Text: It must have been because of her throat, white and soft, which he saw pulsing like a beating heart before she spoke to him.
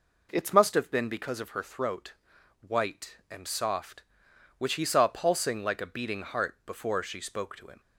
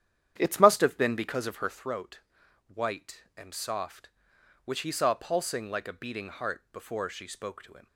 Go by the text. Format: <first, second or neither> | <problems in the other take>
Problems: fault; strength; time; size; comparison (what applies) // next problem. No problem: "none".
first | starts louder than the rest; strong; until 1.8 s; 10 dB